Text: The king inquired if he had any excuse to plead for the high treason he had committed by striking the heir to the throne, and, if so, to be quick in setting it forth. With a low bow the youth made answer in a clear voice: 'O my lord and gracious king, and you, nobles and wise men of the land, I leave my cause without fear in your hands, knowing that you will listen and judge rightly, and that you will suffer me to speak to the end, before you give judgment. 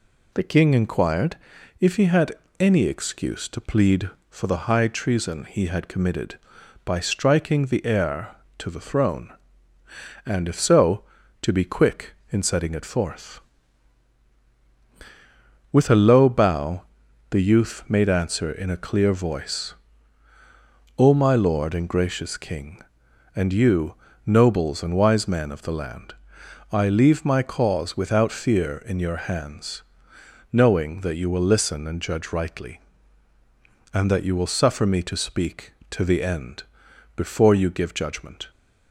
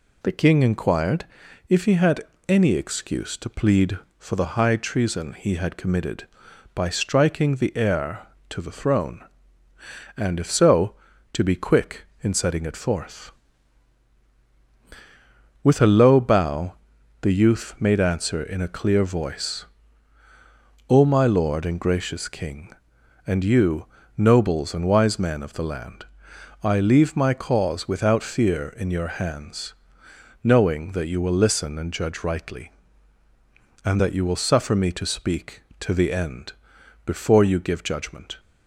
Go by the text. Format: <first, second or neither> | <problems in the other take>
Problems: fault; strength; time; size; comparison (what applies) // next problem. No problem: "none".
neither | pauses between "inquired" and "if"; the same in both // pauses between "had" and "any"; slight; the same in both // pauses between "bow" and "the"; noticeable; the same in both